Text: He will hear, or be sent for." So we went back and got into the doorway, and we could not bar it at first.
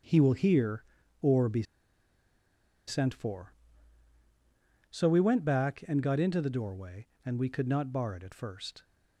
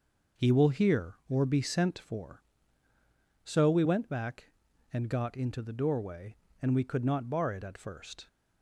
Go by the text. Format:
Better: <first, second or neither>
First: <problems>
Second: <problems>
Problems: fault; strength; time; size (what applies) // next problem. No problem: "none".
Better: second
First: starts louder than the rest; strong; until 1.4 s; 7.5 dB // pauses between "be" and "sent"; strong; at 1.6 s; 1.2 s long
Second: none